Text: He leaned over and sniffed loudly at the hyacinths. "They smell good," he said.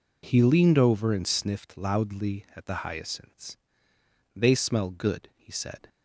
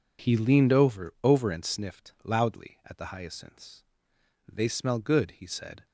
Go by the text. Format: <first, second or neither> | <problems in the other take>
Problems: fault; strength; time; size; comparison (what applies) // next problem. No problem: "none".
first | says "over" twice; at 1.2 s